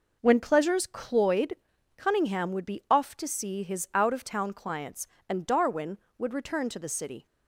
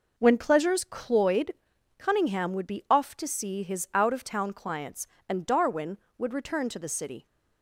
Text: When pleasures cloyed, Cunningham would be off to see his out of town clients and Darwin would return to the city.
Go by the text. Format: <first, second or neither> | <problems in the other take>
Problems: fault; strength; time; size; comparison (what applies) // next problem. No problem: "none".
neither | none